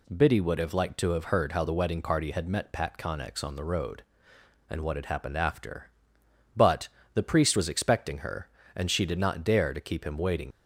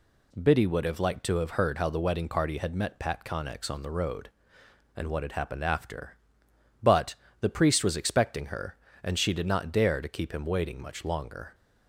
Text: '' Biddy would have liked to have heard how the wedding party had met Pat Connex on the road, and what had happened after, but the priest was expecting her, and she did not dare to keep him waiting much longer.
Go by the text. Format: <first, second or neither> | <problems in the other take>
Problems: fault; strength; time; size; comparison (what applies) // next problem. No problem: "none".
second | pauses between "but" and "the"; slight; at 6.8 s; 0.24 s long; slight in the second // stops before "much longer"; at 10.5 s